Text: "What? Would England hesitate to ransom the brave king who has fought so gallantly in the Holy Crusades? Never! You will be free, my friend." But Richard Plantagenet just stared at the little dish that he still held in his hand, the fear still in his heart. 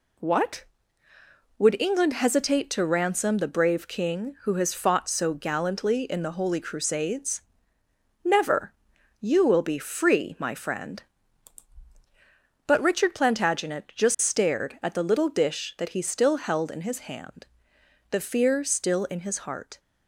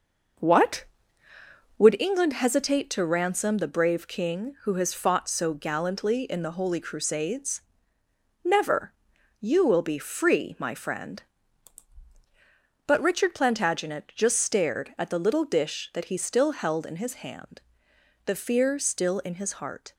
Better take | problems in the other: first | starts louder than the rest; noticeable; until 2.0 s; 6 dB

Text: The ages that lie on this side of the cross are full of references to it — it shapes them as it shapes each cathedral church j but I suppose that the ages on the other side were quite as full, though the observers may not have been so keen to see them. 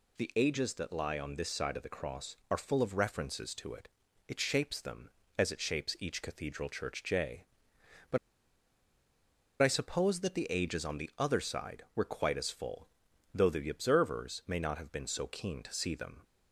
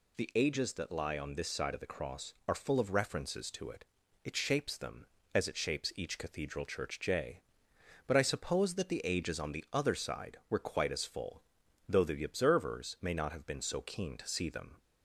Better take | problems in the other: second | pauses between "but" and "I"; strong; at 8.1 s; 1.4 s long

